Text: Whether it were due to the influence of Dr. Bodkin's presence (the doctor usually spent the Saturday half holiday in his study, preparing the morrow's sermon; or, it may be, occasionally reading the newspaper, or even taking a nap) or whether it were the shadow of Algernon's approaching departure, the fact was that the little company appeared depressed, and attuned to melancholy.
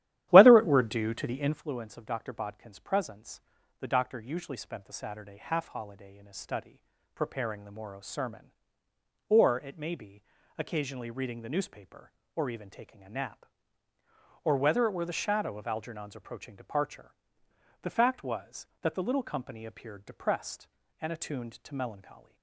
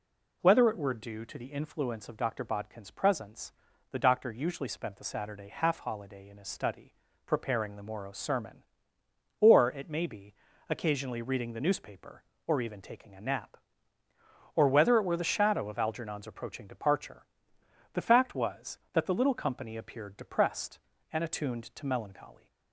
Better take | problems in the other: second | starts louder than the rest; strong; until 1.6 s; 12.5 dB

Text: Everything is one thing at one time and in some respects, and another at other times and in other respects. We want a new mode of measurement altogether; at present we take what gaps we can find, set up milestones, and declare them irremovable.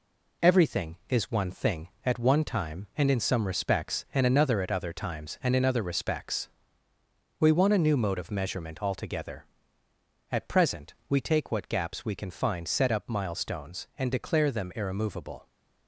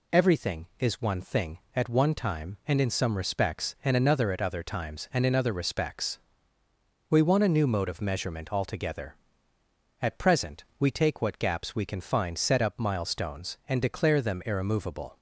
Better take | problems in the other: second | gets quieter; noticeable; throughout; 4 dB // pauses between "present" and "we"; slight; at 10.9 s; 0.16 s long; slight in the second

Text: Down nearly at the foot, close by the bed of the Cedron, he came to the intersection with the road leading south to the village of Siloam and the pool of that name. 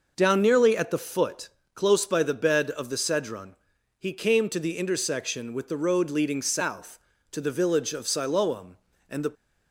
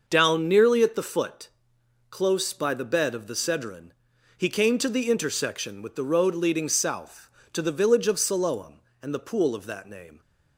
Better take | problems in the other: second | stops before "pool of that name"; at 9.3 s

